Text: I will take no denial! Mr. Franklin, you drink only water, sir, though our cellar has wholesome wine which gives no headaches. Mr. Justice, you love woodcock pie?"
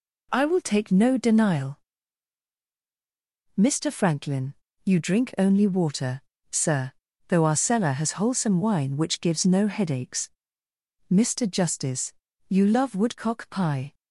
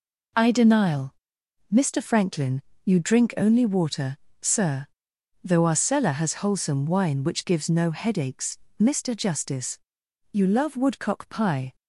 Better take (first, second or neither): first